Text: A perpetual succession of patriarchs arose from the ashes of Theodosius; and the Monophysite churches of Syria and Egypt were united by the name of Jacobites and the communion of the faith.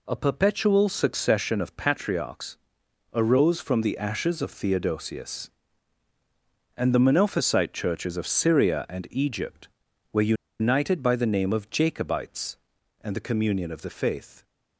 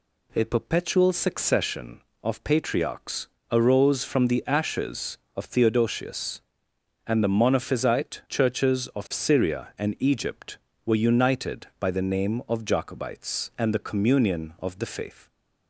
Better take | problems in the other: second | pauses between "patriarchs" and "arose"; noticeable; at 2.5 s; 0.54 s long; slight in the second // pauses between "were" and "united"; slight; at 10.3 s; 0.26 s long

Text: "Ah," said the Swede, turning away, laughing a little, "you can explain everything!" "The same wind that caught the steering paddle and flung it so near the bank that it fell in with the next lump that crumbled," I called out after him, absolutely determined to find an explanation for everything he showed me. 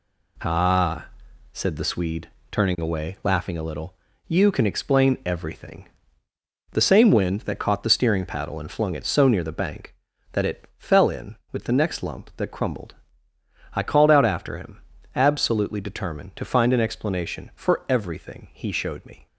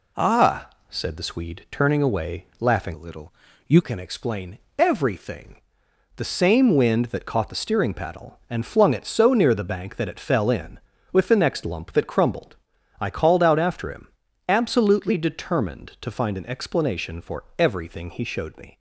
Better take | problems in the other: first | changes voice from "a" to "you"; from 2.9 to 3.8 s; 0.9 s long // pauses between "explain" and "everything"; slight; at 4.5 s; 0.18 s long

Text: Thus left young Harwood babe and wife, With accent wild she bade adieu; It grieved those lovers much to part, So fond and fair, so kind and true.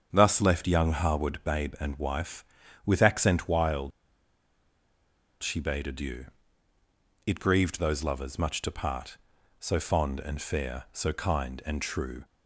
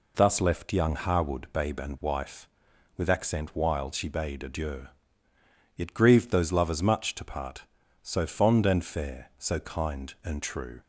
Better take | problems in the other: second | starts louder than the rest; strong; until 1.1 s; 7.5 dB // pauses between "wild" and "she"; strong; at 3.9 s; 1.5 s long

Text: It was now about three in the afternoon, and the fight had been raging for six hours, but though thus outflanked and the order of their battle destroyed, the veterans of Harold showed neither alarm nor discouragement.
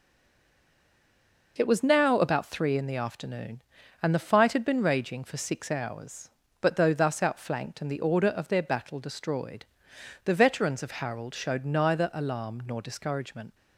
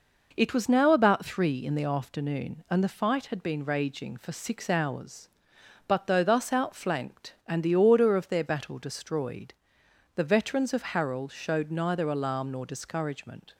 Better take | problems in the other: second | stays silent before the first word; noticeable; until 1.5 s; 1.5 s long

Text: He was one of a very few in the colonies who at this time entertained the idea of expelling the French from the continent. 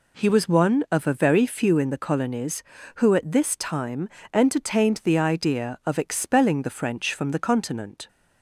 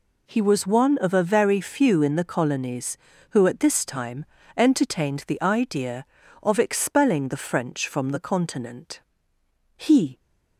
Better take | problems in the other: first | pauses between "time" and "entertained"; slight; at 4.2 s; 0.32 s long; slight in the first // goes on to say "He"; slight; from 9.7 s on; 0.42 s long

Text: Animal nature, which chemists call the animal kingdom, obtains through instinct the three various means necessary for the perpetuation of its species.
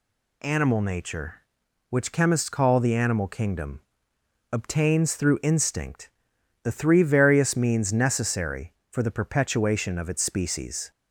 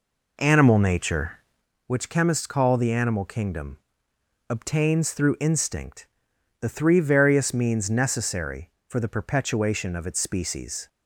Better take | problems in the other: first | starts louder than the rest; until 1.7 s; 3.5 dB // pauses between "instinct" and "the"; noticeable; at 6.0 s; 0.52 s long; noticeable in the first

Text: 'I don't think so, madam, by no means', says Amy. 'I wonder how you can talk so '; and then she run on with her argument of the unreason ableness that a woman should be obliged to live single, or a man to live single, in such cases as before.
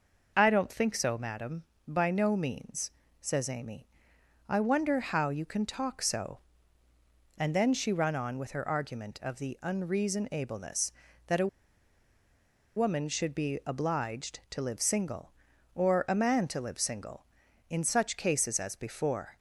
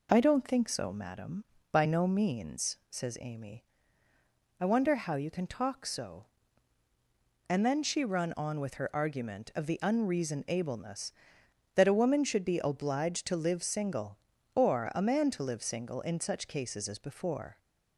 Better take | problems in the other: second | pauses between "a" and "woman"; strong; at 11.4 s; 1.2 s long

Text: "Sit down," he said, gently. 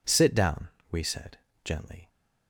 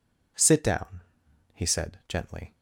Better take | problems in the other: second | says "we" for "he"; at 0.9 s

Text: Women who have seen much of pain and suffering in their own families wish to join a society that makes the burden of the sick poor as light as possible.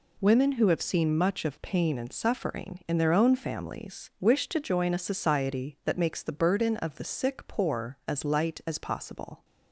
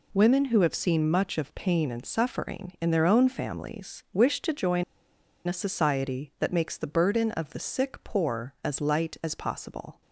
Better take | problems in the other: first | pauses between "join" and "a"; noticeable; at 4.8 s; 0.63 s long

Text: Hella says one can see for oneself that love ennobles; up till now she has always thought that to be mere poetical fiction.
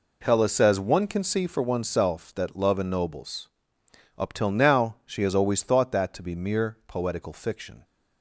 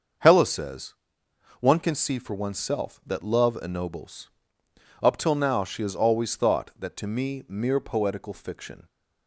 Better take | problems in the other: first | starts louder than the rest; until 1.8 s; 6.5 dB // pauses between "says" and "one"; noticeable; at 0.9 s; 0.66 s long // says "me" for "be"; at 7.0 s

